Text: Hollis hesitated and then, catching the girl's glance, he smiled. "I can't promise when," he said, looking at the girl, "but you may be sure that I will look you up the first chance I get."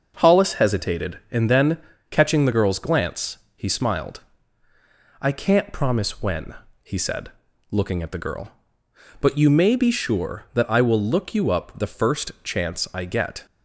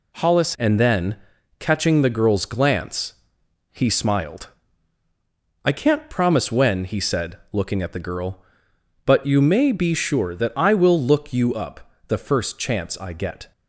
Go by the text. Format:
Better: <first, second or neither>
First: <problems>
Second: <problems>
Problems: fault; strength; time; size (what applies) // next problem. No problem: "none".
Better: first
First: none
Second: skips "hesitated"; at 0.5 s // pauses between "up" and "the"; slight; at 11.9 s; 0.16 s long